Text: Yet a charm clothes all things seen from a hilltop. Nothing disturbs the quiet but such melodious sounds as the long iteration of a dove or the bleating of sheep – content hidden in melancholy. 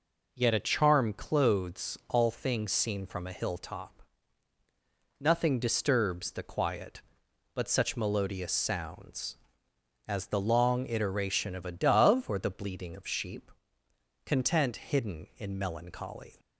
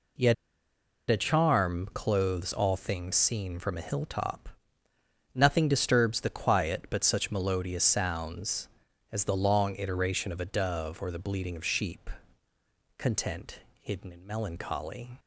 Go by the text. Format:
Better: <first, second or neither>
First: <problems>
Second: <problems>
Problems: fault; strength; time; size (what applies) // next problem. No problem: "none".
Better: first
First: none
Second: pauses between "Yet" and "a"; noticeable; at 0.3 s; 0.76 s long // pauses between "content" and "hidden"; slight; at 13.5 s; 0.22 s long